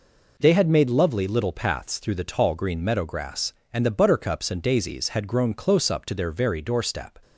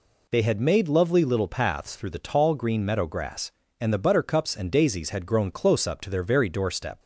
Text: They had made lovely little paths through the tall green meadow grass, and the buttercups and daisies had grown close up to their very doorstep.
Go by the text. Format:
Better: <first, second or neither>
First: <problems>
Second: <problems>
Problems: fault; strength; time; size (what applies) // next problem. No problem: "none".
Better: neither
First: none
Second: none